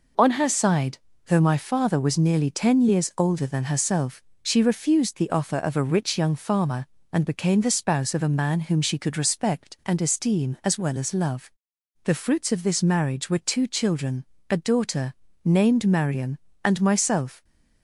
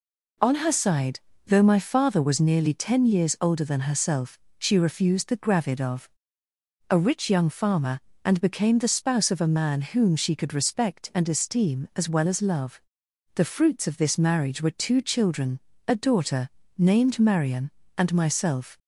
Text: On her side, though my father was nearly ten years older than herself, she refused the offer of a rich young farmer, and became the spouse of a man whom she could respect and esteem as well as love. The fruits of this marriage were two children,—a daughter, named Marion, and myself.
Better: first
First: none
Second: says "gravid" for "offer"; at 5.3 s // pauses between "of" and "a"; noticeable; at 6.0 s; 0.84 s long

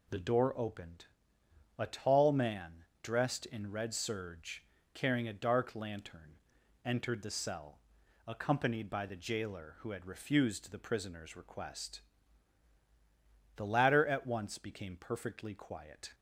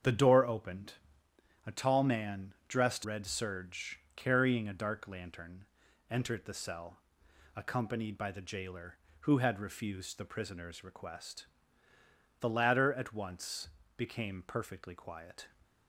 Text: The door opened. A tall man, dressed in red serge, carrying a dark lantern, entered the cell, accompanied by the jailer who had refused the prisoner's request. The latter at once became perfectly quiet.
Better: first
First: none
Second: starts louder than the rest; strong; until 1.7 s; 7.5 dB // skips "in"; at 3.0 s // pauses between "once" and "became"; slight; at 13.6 s; 0.28 s long

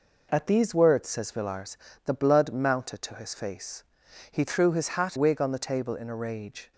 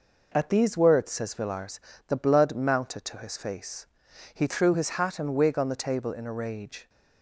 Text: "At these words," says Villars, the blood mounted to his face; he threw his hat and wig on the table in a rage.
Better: second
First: skips "and"; at 5.1 s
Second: none

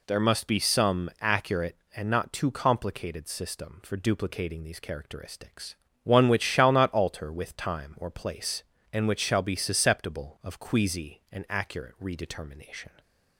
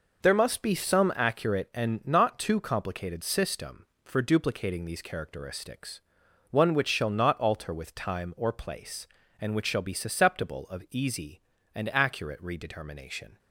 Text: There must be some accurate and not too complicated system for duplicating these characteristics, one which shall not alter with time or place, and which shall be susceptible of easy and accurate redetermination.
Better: second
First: says "queasy" for "easy"; at 10.5 s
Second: none

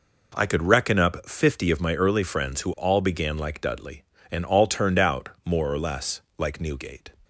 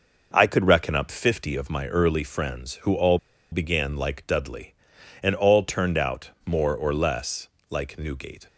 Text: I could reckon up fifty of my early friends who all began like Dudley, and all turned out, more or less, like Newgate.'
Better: first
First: none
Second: pauses between "all" and "began"; slight; at 3.1 s; 0.33 s long

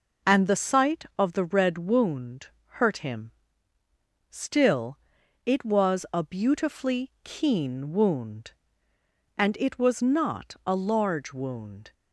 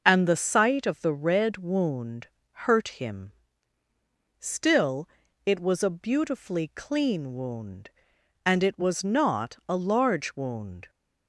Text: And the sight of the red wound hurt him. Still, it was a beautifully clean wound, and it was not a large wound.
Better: second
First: pauses between "wound" and "hurt"; slight; at 2.4 s; 0.30 s long // says "keen" for "clean"; at 7.2 s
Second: pauses between "wound" and "hurt"; slight; at 2.2 s; 0.24 s long

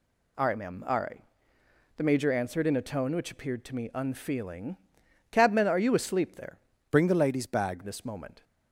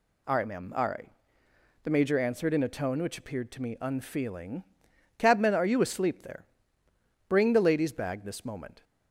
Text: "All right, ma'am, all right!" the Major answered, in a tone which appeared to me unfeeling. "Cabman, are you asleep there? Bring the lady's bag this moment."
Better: second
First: changes voice from "Bring" to "bag"; from 6.8 to 7.8 s; 1.0 s long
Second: none

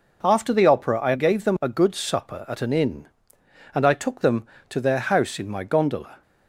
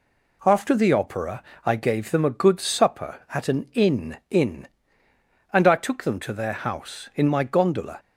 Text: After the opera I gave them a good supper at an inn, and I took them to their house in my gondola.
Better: first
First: none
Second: pauses between "opera" and "I"; slight; at 1.4 s; 0.22 s long // says "inn" twice; at 4.2 s

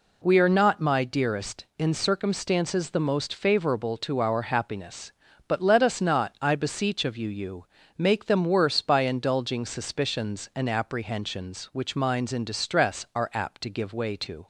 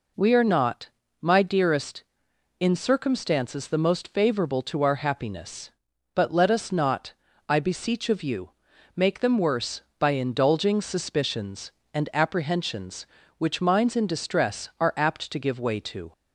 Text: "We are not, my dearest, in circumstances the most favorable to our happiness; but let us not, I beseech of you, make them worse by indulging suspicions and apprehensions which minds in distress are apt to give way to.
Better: second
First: says "you" twice; at 7.2 s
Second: none

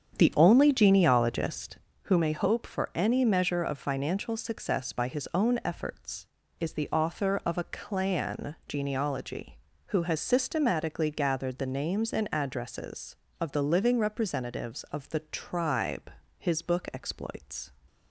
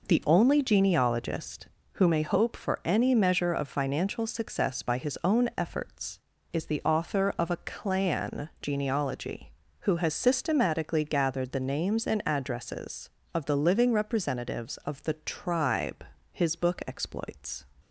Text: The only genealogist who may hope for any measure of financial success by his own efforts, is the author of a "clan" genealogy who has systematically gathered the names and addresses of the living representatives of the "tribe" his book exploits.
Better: second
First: starts louder than the rest; strong; until 2.0 s; 8 dB // pauses between "tribe" and "his"; slight; at 16.1 s; 0.28 s long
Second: pauses between "tribe" and "his"; slight; at 16.0 s; 0.28 s long

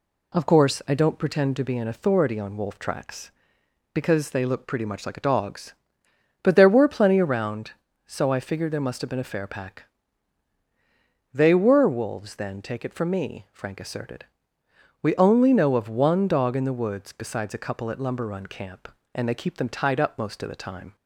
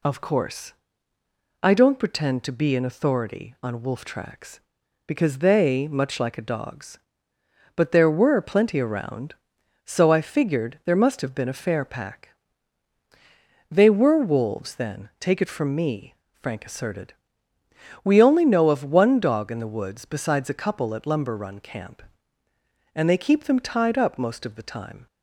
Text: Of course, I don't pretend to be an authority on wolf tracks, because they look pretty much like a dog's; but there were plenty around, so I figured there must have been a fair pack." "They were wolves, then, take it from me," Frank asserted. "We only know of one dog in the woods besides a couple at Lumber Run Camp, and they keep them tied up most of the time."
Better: first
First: none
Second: skips "look pretty"; at 5.8 s

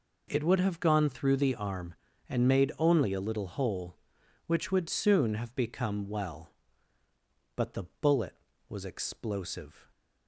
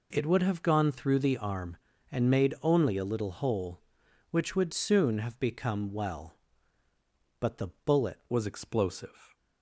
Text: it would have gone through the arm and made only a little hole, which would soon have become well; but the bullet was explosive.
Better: first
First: pauses between "the" and "bullet"; slight; at 7.8 s; 0.18 s long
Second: pauses between "the" and "bullet"; slight; at 7.6 s; 0.18 s long // changes voice at "was"; from 8.3 s on; 1.0 s long

